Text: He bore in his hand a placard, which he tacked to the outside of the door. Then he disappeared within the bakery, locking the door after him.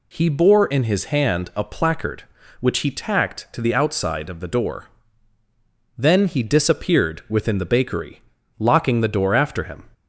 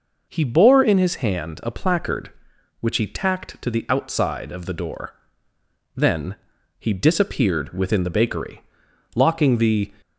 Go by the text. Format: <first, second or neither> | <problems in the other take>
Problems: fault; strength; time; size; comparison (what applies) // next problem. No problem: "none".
first | pauses between "Then" and "he"; at 6.3 s; 0.42 s long // stops before "door after him"; at 10.0 s